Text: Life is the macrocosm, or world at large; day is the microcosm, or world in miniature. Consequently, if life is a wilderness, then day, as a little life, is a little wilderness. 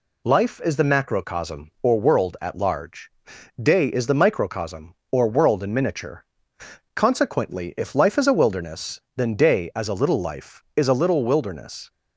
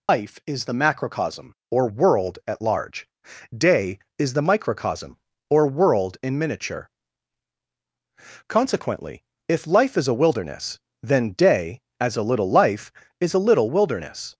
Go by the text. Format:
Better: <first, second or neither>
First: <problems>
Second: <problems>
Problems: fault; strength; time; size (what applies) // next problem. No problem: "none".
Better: first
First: none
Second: loses the start of "Life"; at 0.0 s; 105 ms